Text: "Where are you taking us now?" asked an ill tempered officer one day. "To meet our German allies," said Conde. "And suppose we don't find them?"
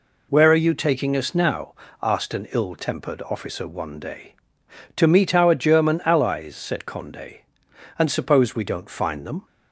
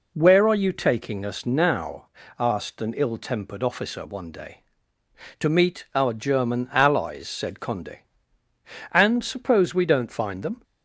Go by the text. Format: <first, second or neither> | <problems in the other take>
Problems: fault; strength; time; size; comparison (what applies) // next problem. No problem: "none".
neither | none